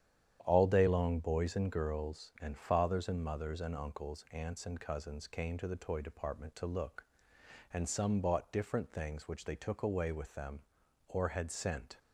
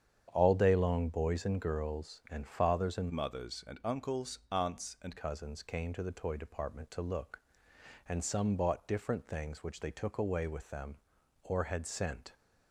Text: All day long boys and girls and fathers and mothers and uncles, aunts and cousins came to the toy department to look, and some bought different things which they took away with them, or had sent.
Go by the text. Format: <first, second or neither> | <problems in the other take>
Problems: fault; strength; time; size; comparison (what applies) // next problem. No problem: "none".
first | starts louder than the rest; strong; until 1.3 s; 8.5 dB; strong in the first // changes voice from "mothers" to "and"; from 3.1 to 5.1 s; 2.0 s long